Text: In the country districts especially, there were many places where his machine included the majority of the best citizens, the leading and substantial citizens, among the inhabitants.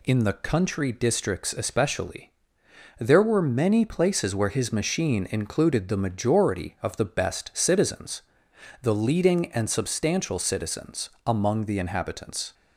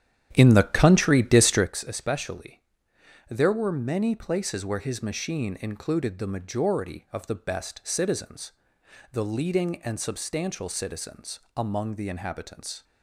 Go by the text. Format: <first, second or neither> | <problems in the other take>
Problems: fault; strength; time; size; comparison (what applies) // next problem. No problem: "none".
first | starts louder than the rest; strong; until 1.8 s; 10 dB